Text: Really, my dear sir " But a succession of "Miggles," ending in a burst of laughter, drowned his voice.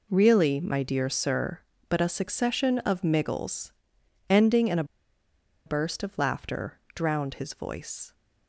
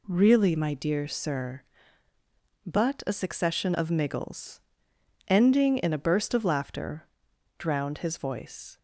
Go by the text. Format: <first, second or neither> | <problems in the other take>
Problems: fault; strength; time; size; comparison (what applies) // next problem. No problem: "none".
second | pauses between "a" and "burst"; noticeable; at 4.8 s; 0.82 s long